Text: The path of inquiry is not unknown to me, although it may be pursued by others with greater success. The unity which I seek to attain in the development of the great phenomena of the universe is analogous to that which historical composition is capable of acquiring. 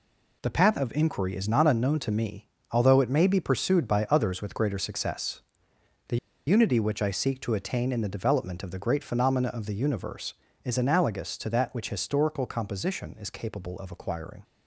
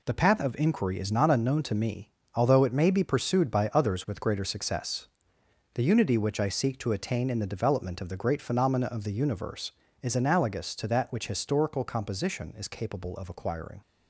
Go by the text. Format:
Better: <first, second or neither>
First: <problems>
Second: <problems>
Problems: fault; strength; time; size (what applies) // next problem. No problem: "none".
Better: second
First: pauses between "The" and "unity"; slight; at 6.1 s; 0.30 s long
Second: none